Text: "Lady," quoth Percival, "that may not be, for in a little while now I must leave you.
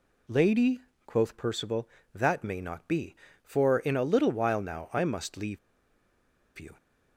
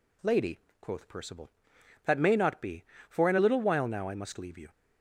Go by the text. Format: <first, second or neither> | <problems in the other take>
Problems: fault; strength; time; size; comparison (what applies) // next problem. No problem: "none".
second | pauses between "leave" and "you"; at 5.5 s; 0.99 s long